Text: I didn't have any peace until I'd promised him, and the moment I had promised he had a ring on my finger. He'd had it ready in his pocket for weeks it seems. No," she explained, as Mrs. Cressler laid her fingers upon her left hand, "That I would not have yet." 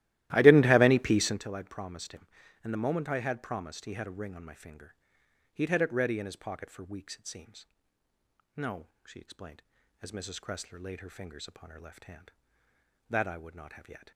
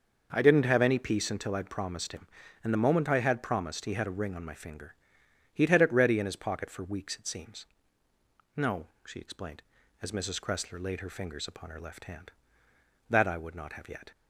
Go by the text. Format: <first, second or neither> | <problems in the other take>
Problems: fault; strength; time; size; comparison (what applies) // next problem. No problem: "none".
second | starts louder than the rest; strong; until 1.4 s; 15 dB